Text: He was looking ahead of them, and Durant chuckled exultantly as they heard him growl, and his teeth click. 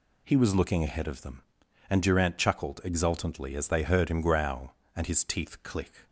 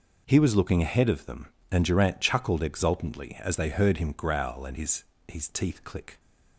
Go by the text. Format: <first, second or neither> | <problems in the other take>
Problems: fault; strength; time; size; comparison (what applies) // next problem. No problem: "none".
first | says "his" twice; at 5.2 s